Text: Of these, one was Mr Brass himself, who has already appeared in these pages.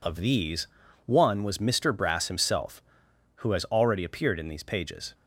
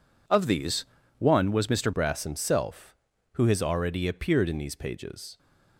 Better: first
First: none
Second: changes voice at "Brass"; from 1.9 s on; 3.4 s long

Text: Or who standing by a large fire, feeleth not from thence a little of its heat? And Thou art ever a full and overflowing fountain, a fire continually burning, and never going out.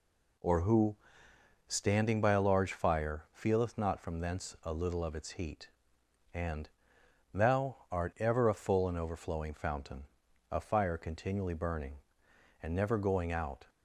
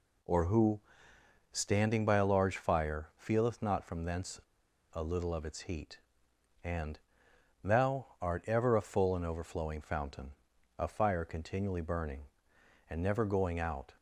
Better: first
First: pauses between "who" and "standing"; noticeable; at 0.9 s; 0.72 s long // pauses between "And" and "Thou"; noticeable; at 6.6 s; 0.64 s long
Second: pauses between "who" and "standing"; noticeable; at 0.7 s; 0.72 s long // pauses between "thence" and "a"; noticeable; at 4.3 s; 0.51 s long // pauses between "And" and "Thou"; noticeable; at 6.9 s; 0.64 s long

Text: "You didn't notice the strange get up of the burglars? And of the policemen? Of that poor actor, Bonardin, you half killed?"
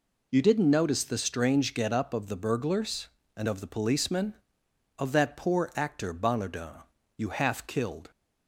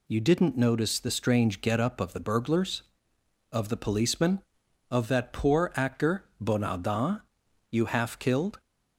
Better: first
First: none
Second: skips "And"; at 3.1 s

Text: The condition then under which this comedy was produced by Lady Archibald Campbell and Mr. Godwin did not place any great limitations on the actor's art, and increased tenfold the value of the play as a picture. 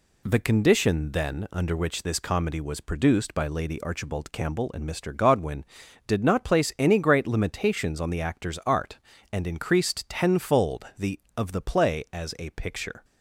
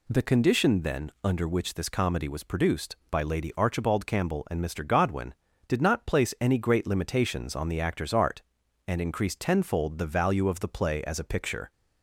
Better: second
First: skips "value"; at 11.2 s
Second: none

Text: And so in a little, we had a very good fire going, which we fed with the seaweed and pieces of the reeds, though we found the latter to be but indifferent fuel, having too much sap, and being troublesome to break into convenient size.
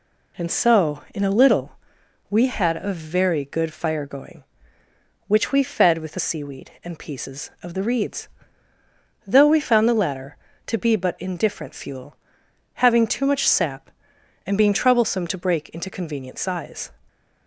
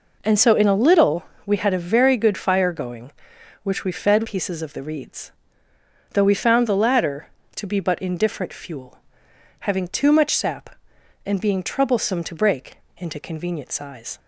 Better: first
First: none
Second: skips "with the seaweed and"; at 4.2 s // pauses between "break" and "into"; slight; at 12.7 s; 0.22 s long

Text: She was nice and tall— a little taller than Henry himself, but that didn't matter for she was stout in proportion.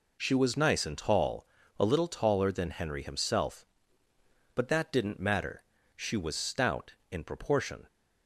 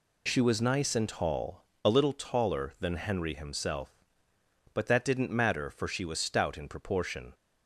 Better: second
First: skips "for"; at 5.7 s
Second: none

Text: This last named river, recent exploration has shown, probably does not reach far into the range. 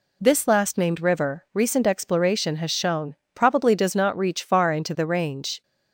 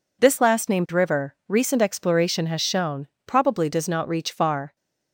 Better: first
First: none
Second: stops before "into the range"; at 4.7 s

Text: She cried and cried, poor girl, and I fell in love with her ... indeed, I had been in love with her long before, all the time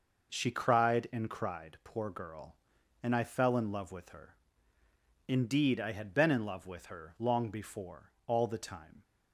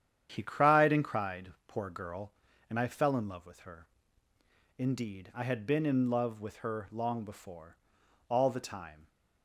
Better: first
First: none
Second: starts louder than the rest; strong; until 1.3 s; 9 dB // says "He" for "She"; at 0.3 s

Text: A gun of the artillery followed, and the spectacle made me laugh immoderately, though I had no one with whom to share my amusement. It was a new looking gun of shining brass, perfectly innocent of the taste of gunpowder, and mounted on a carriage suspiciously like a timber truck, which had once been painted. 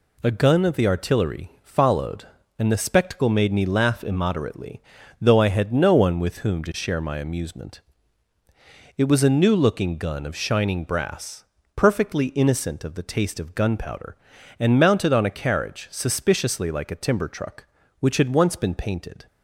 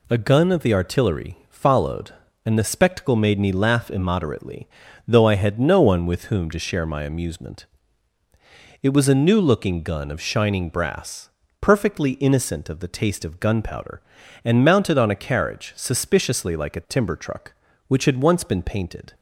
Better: neither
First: none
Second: none

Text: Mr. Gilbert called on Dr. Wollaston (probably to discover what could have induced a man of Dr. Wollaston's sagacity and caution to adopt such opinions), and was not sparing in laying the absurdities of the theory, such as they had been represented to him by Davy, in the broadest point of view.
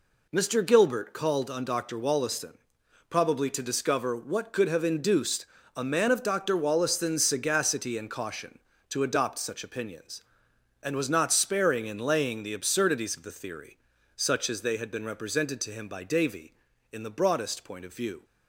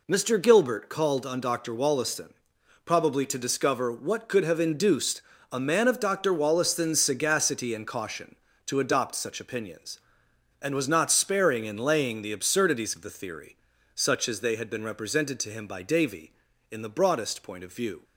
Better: neither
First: pauses between "induced" and "a"; slight; at 5.4 s; 0.28 s long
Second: pauses between "induced" and "a"; slight; at 5.2 s; 0.28 s long

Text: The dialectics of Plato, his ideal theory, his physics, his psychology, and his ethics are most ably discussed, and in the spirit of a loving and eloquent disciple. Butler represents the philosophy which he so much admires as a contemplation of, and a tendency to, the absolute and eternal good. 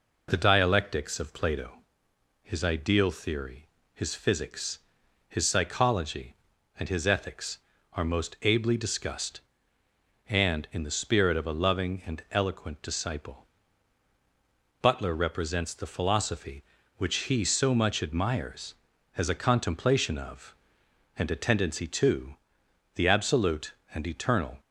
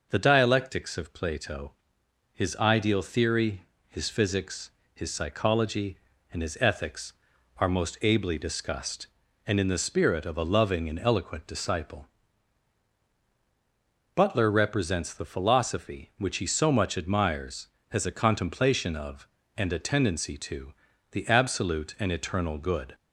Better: second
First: stops before "good"; at 24.6 s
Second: none

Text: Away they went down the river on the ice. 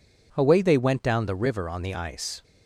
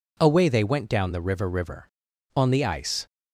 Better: first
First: none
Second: says "river" twice; at 1.4 s

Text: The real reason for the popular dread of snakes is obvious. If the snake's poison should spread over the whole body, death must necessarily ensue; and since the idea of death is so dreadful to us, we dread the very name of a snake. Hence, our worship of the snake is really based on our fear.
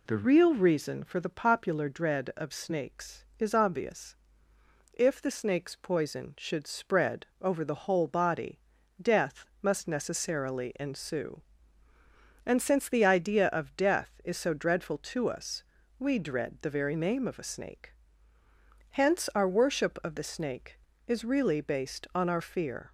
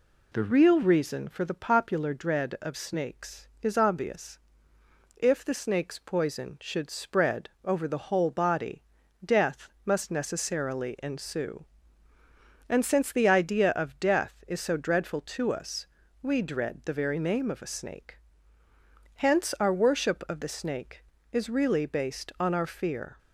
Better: neither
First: pauses between "death" and "must"; slight; at 9.4 s; 0.16 s long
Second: pauses between "death" and "must"; slight; at 9.6 s; 0.16 s long

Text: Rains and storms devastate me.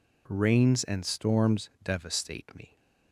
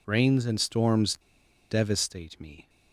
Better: first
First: none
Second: pauses between "storms" and "devastate"; noticeable; at 1.1 s; 0.54 s long

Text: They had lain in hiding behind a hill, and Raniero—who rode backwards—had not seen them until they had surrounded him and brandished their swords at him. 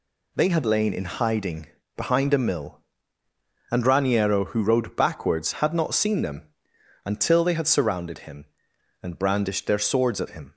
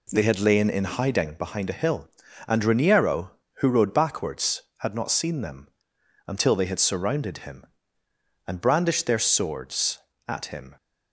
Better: second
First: pauses between "hiding" and "behind"; slight; at 1.6 s; 0.28 s long // says "mill" for "hill"; at 2.3 s // pauses between "them" and "until"; noticeable; at 6.4 s; 0.58 s long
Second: pauses between "them" and "until"; noticeable; at 5.6 s; 0.58 s long

